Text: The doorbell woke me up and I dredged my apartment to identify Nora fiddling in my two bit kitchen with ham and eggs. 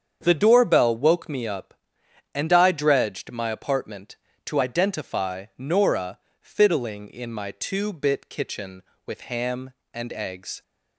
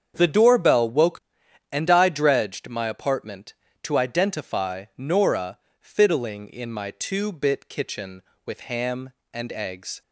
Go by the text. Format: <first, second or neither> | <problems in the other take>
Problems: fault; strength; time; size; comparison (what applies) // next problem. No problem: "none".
first | starts louder than the rest; strong; until 1.1 s; 7.5 dB; strong in the first // skips "me up"; at 1.4 s // pauses between "Nora" and "fiddling"; slight; at 5.5 s; 0.24 s long; slight in the first